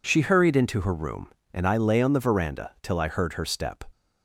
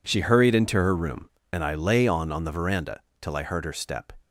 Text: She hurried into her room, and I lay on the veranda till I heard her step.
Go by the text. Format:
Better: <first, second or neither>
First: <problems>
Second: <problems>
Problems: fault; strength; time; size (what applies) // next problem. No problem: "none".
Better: first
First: none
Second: says "on" twice; at 2.3 s // pauses between "veranda" and "till"; slight; at 2.9 s; 0.22 s long